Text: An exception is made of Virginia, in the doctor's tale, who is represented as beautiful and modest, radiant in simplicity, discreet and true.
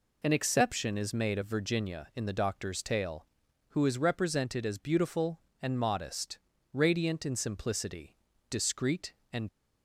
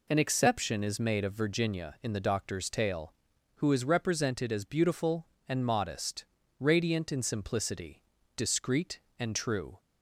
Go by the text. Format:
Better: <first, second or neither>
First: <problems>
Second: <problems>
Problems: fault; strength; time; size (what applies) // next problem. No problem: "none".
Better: second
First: stops before "true"; at 9.4 s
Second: none